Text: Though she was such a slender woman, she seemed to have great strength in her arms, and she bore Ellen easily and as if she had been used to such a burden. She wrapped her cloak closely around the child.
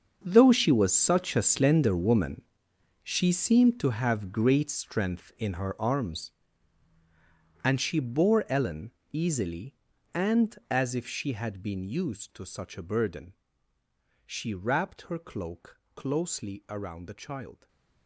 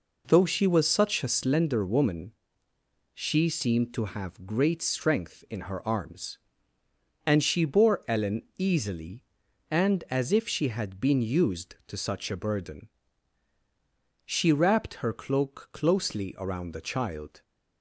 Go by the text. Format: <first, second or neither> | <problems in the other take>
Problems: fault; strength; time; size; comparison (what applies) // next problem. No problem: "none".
second | gets quieter; strong; throughout; 16 dB // pauses between "Ellen" and "easily"; slight; at 8.9 s; 0.20 s long; slight in the second // pauses between "cloak" and "closely"; slight; at 15.7 s; 0.16 s long // stays silent after the last word; slight; from 17.5 s on; 0.5 s long